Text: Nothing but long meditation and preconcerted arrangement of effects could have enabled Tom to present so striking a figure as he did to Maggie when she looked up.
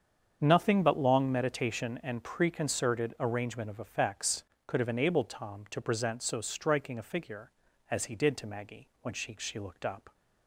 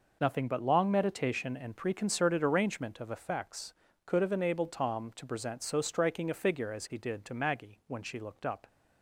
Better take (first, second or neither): second